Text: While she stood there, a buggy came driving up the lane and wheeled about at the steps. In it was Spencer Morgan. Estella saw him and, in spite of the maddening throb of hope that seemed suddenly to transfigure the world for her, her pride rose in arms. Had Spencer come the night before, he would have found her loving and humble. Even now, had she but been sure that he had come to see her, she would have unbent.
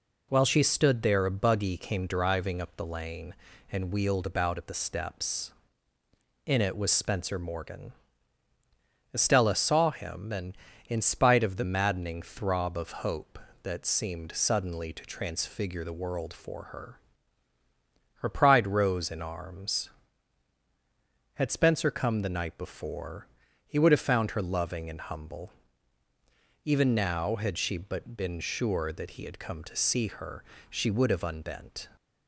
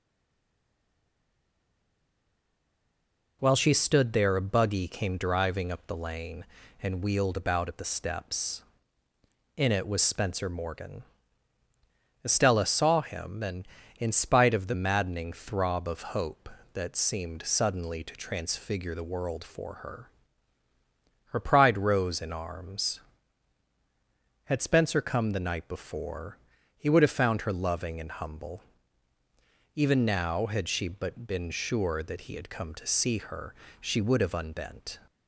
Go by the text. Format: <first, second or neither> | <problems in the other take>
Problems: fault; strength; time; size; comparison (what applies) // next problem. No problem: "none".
first | stays silent before the first word; strong; until 3.3 s; 3.3 s long